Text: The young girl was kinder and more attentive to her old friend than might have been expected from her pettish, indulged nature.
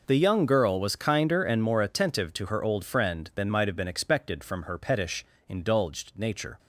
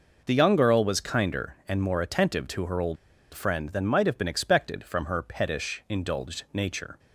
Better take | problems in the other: first | pauses between "old" and "friend"; at 2.9 s; 0.36 s long

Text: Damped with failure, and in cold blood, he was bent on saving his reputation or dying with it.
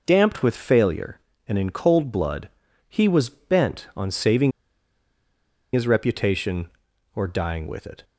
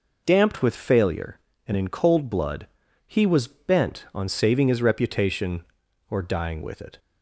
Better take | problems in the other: second | pauses between "saving" and "his"; at 4.5 s; 1.2 s long

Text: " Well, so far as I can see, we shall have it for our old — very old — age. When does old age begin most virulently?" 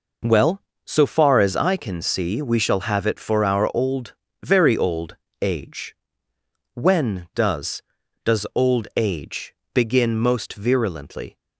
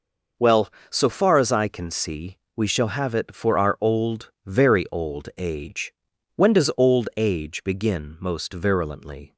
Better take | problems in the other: second | says "does" twice; at 8.2 s // pauses between "age" and "begin"; slight; at 9.5 s; 0.20 s long

